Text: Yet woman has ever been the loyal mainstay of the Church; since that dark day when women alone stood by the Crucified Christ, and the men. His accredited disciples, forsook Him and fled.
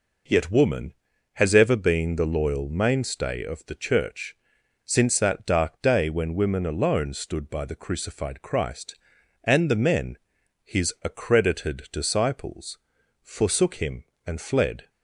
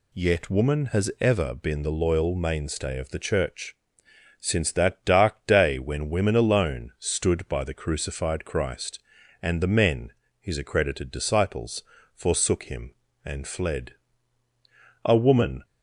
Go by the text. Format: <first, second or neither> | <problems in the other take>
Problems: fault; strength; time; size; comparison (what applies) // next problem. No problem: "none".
first | goes on to say "A woman"; from 15.0 s on; 0.58 s long